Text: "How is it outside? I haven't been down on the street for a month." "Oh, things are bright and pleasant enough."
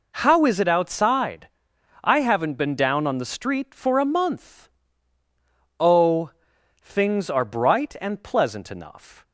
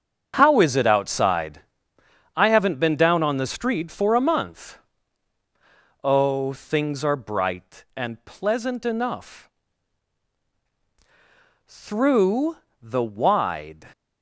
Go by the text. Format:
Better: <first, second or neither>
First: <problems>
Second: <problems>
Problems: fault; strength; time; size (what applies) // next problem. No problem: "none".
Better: first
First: none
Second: starts louder than the rest; strong; until 1.4 s; 7.5 dB // goes on to say "Through the wide"; strong; from 11.6 s on; 2.2 s long